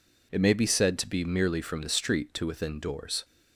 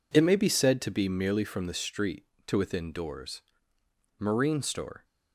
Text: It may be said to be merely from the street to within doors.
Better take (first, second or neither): first